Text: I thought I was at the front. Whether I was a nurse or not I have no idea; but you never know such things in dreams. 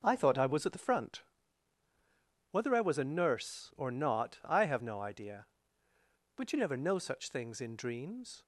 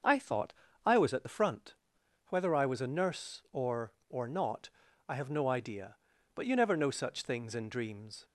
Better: first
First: none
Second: starts louder than the rest; noticeable; until 1.3 s; 6 dB // pauses between "thought" and "I"; slight; at 0.5 s; 0.34 s long // says "or" twice; at 4.0 s // pauses between "not" and "I"; at 4.6 s; 0.40 s long

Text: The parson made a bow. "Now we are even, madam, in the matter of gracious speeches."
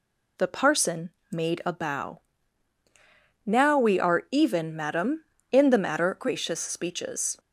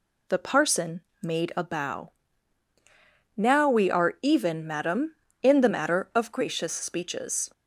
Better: second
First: pauses between "parson" and "made"; slight; at 1.1 s; 0.20 s long // skips "of"; at 6.1 s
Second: pauses between "parson" and "made"; slight; at 1.0 s; 0.20 s long

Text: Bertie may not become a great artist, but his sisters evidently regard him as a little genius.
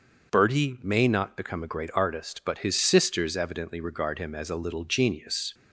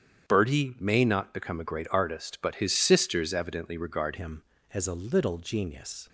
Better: first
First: starts louder than the rest; until 1.3 s; 6.5 dB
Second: starts louder than the rest; strong; until 1.3 s; 8.5 dB // changes voice at "him"; from 4.1 s on; 1.9 s long

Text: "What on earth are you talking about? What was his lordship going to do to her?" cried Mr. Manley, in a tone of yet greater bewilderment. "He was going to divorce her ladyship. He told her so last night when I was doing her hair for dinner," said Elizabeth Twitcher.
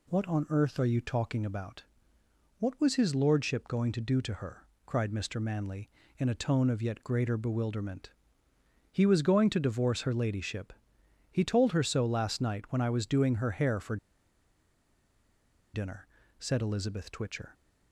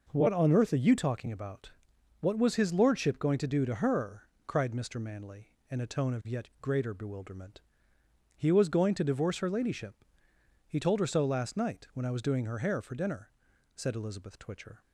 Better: second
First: pauses between "for" and "dinner"; strong; at 13.9 s; 1.7 s long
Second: none

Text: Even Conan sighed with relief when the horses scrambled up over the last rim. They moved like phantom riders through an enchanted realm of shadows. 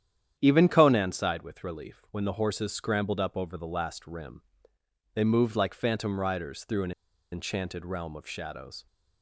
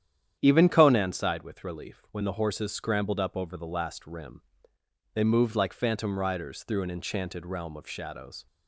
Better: second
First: starts louder than the rest; strong; until 1.4 s; 9.5 dB // pauses between "an" and "enchanted"; at 6.9 s; 0.40 s long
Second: starts louder than the rest; strong; until 1.4 s; 9.5 dB

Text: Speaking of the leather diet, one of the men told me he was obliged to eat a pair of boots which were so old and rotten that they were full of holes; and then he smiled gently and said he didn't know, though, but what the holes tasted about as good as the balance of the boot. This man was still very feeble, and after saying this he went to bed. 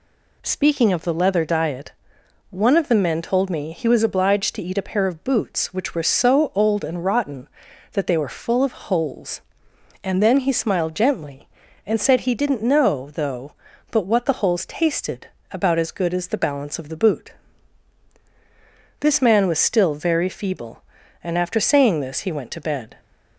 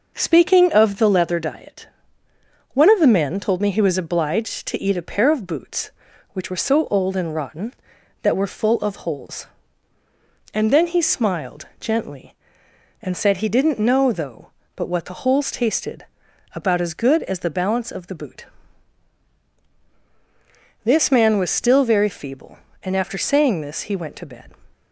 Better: first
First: pauses between "tasted" and "about"; slight; at 15.2 s; 0.26 s long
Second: skips "they"; at 8.3 s // pauses between "tasted" and "about"; noticeable; at 16.0 s; 0.50 s long

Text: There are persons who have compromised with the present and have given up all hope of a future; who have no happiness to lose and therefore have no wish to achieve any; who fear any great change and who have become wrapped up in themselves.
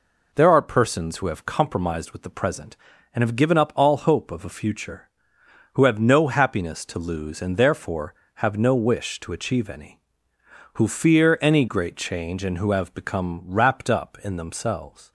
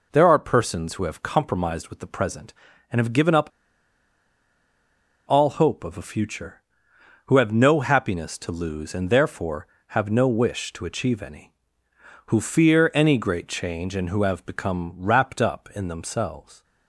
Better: first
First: none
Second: pauses between "up" and "all"; strong; at 3.4 s; 1.8 s long

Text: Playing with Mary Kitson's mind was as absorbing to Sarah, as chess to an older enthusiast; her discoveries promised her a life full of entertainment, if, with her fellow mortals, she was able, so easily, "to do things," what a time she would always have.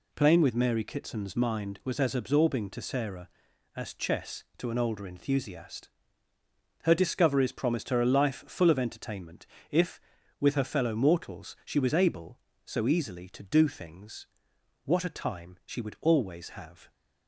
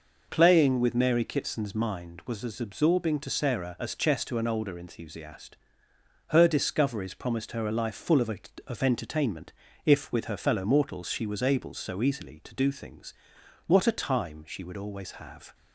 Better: first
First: none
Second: says "of" twice; at 8.6 s

